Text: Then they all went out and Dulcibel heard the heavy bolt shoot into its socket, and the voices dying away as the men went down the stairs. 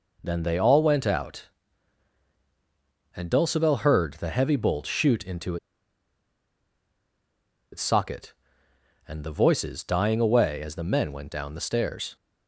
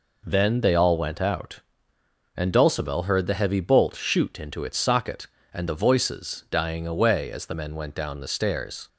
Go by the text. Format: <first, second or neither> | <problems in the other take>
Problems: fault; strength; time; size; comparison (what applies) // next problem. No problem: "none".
second | pauses between "into" and "its"; strong; at 5.5 s; 2.1 s long